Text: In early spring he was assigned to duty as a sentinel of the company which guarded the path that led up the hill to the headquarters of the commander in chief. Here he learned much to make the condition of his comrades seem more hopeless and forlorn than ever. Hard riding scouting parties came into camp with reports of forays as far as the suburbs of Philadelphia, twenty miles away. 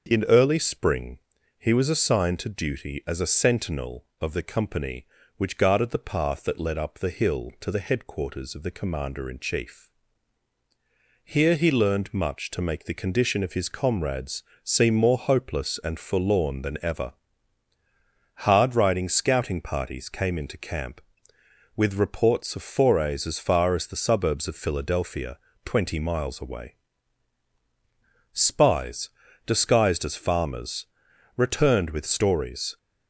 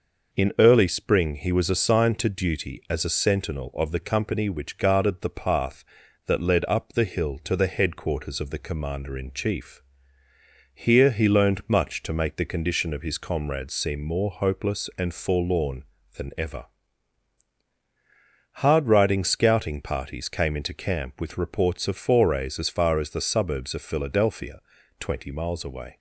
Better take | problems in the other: second | starts louder than the rest; until 1.1 s; 6.5 dB // pauses between "spring" and "he"; at 1.1 s; 0.40 s long // pauses between "comrades" and "seem"; slight; at 14.4 s; 0.20 s long // goes on to say "Spies disguised as farmers returned with stories"; strong; from 28.3 s on; 4.4 s long

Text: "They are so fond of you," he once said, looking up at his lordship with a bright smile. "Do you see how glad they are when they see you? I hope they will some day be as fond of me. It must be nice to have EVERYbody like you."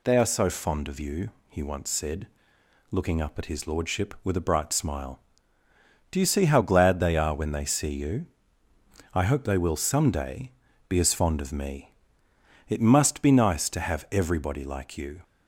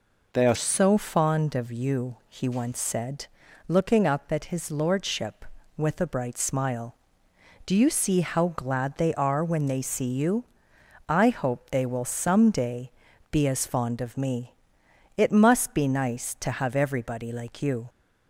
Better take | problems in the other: first | changes voice at "so"; from 0.5 s on; 17.3 s long // pauses between "day" and "be"; at 12.9 s; 0.40 s long; slight in the first

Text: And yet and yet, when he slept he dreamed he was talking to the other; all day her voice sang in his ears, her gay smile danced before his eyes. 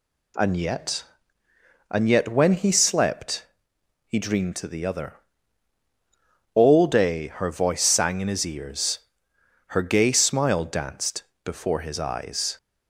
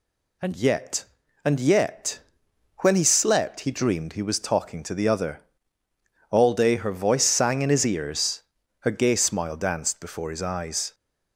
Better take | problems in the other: second | pauses between "slept" and "he"; noticeable; at 3.4 s; 0.62 s long // skips "he was talking"; at 4.5 s // pauses between "danced" and "before"; slight; at 11.2 s; 0.22 s long

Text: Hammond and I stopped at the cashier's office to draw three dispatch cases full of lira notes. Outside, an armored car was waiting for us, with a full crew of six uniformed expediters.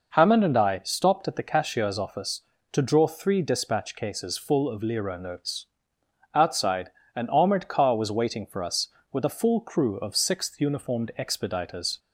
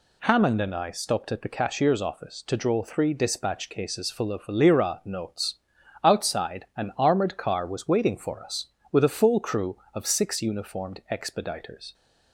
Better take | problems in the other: second | says "sixth" for "six"; at 10.1 s

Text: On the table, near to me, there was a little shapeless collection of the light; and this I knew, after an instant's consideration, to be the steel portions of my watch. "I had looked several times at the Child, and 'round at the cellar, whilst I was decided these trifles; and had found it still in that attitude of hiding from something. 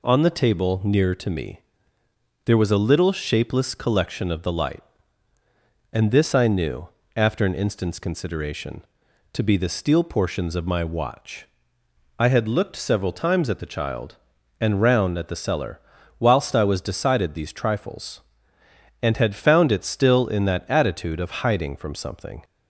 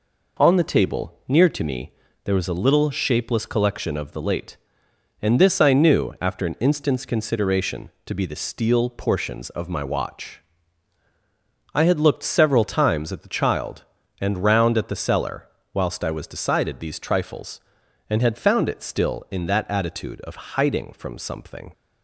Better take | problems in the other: first | says "late" for "light"; at 4.2 s

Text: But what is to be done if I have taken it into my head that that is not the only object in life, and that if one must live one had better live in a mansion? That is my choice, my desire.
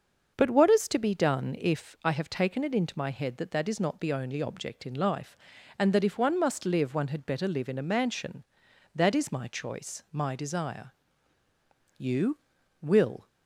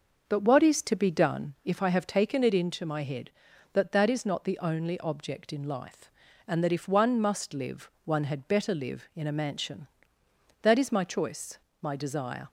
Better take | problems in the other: second | starts louder than the rest; until 1.3 s; 6.5 dB; also in the second // goes on to say "You will"; noticeable; from 11.9 s on; 1.3 s long

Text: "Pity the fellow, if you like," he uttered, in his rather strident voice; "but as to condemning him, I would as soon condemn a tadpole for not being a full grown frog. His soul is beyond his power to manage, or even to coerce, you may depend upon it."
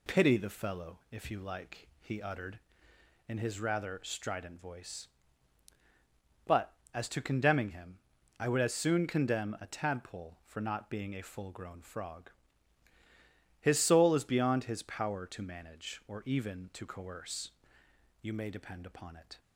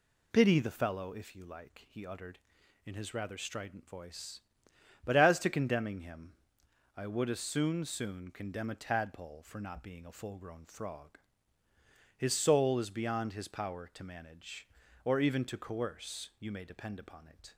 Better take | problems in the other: first | says "soon" twice; at 7.8 s

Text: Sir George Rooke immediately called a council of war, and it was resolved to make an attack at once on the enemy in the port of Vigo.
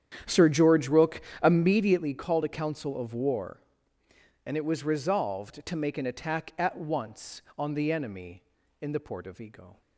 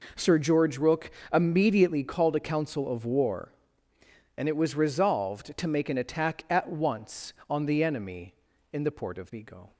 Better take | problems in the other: second | starts louder than the rest; strong; until 1.8 s; 9.5 dB // pauses between "Rooke" and "immediately"; slight; at 1.2 s; 0.22 s long; slight in the second

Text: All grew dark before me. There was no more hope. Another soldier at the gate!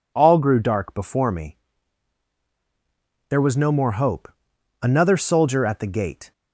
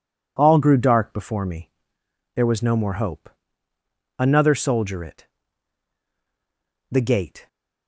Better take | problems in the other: first | says "it" for "at"; at 5.0 s

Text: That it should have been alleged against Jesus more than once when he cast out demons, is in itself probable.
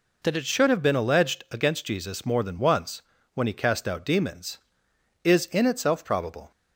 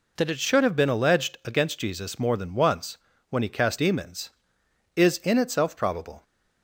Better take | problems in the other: first | pauses between "once" and "when"; slight; at 2.9 s; 0.32 s long; slight in the first // skips "out"; at 3.7 s

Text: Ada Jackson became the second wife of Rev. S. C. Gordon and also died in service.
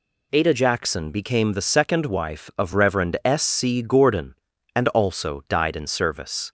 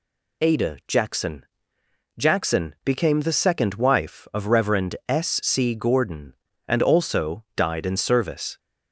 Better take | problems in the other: first | says "Jackson" twice; at 2.1 s

